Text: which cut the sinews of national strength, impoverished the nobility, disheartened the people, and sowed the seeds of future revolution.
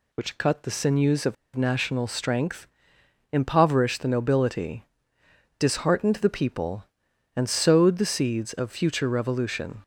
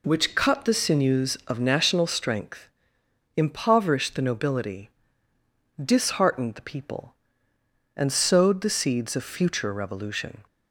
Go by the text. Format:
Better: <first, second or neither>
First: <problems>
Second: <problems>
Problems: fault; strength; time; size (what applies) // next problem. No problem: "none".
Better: second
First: pauses between "of" and "national"; slight; at 1.3 s; 0.21 s long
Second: none